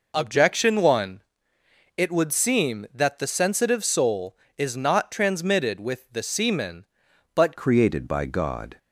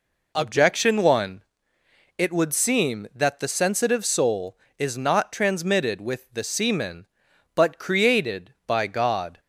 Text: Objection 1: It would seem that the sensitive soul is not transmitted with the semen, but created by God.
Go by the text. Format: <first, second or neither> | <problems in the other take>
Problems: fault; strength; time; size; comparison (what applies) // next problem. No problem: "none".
second | changes voice at "created"; from 7.5 s on; 1.2 s long